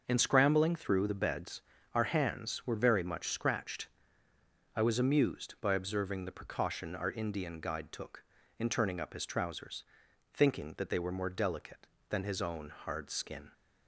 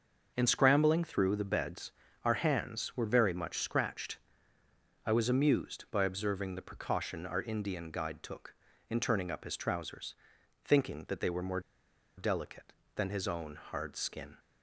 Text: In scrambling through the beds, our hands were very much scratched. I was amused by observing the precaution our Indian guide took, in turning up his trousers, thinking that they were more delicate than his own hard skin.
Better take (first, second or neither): first